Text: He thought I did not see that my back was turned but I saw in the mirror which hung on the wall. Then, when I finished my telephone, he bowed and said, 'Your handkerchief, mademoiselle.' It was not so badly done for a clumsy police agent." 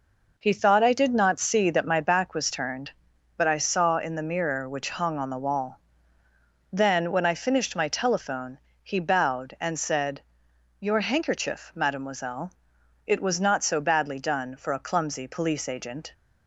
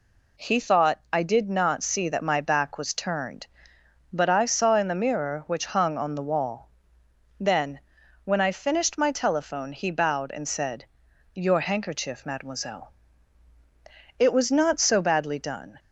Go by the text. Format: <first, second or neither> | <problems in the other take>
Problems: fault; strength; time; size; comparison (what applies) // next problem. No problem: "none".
first | stops before "for a clumsy police agent"; at 15.7 s